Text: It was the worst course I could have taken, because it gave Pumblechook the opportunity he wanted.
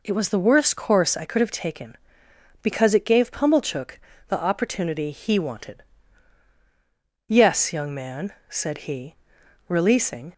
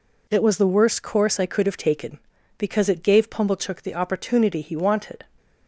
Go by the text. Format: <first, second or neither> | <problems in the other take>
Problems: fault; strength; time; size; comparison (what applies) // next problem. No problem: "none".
second | pauses between "Pumblechook" and "the"; slight; at 3.9 s; 0.30 s long // goes on to say "Yes young man said he releasing"; strong; from 7.2 s on; 3.0 s long